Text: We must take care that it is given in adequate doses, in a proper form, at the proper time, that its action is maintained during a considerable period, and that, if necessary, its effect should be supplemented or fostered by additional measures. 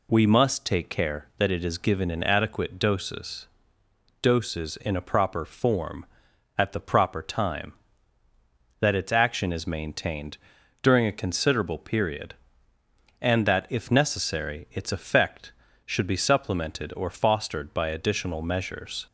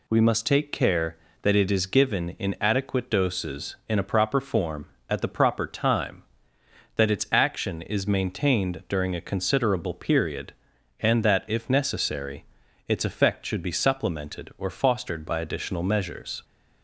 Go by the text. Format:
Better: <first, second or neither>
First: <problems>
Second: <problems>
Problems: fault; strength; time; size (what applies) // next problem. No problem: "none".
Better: second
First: says "doses" twice; at 4.2 s // pauses between "maintained" and "during"; noticeable; at 10.3 s; 0.46 s long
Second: none